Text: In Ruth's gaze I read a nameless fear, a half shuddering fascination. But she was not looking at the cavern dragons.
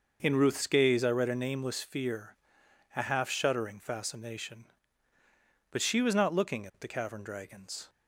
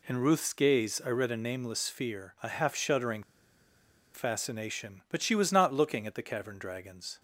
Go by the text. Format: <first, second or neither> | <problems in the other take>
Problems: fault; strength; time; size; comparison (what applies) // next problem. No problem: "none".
first | pauses between "shuddering" and "fascination"; noticeable; at 3.2 s; 0.91 s long